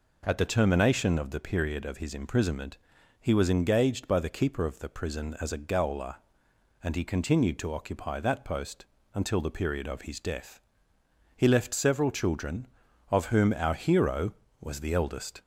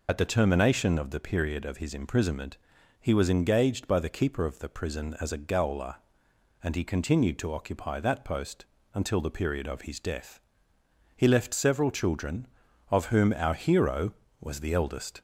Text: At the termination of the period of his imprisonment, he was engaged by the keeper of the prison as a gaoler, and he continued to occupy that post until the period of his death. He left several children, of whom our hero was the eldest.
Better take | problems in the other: first | loses the start of "At"; at 0.0 s; 60 ms // pauses between "post" and "until"; slight; at 8.6 s; 0.28 s long; slight in the first

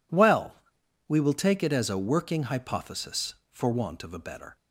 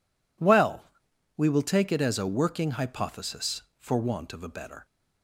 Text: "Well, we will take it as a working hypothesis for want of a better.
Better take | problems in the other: neither | none

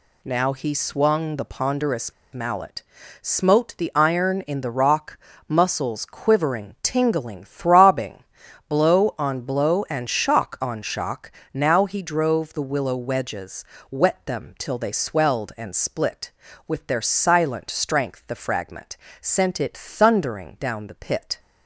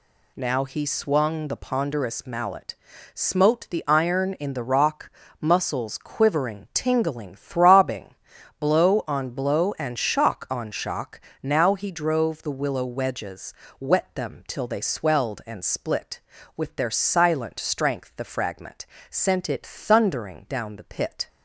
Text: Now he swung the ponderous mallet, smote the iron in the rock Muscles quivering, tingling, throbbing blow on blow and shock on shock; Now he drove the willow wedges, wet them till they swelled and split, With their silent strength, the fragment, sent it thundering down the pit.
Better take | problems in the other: second | pauses between "ponderous" and "mallet"; slight; at 2.1 s; 0.19 s long // pauses between "rock" and "Muscles"; slight; at 5.1 s; 0.30 s long; slight in the second // pauses between "throbbing" and "blow"; noticeable; at 8.2 s; 0.46 s long; noticeable in the second

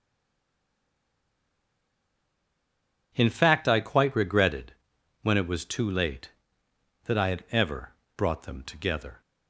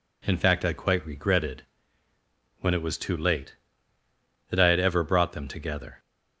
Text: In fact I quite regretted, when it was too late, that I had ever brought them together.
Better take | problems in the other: second | stays silent before the first word; strong; until 3.1 s; 3.1 s long // pauses between "ever" and "brought"; slight; at 7.9 s; 0.24 s long

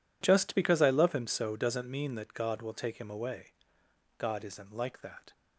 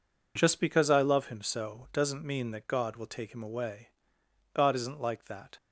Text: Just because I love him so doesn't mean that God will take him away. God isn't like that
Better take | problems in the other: neither | none

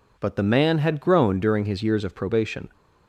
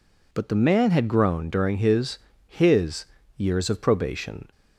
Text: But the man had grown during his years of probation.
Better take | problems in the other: first | says "his" twice; at 2.4 s

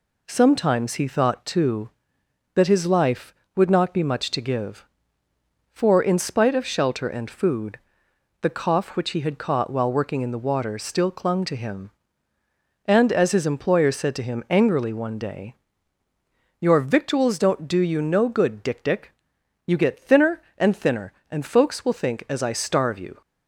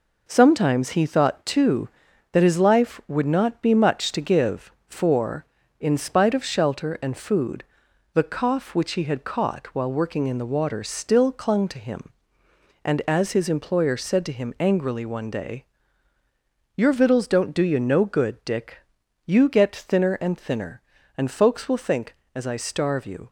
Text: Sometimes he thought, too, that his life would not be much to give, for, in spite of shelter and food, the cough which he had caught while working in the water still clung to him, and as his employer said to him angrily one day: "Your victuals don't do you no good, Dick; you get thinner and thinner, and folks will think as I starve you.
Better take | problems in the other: second | says "Dick" twice; at 18.8 s

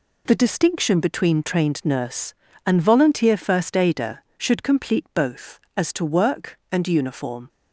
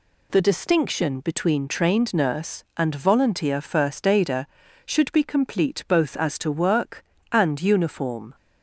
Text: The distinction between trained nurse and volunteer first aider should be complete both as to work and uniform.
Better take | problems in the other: second | skips "be"; at 4.6 s

